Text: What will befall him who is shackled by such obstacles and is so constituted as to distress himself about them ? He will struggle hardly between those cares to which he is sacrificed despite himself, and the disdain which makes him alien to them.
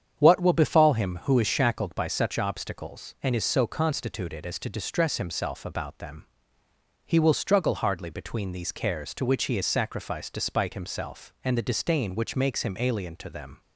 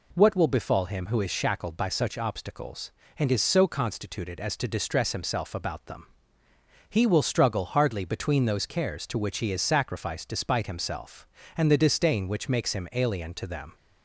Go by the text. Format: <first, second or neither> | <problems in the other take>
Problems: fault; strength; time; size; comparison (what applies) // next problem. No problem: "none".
second | starts louder than the rest; strong; until 1.2 s; 8 dB // says "these" for "those"; at 8.5 s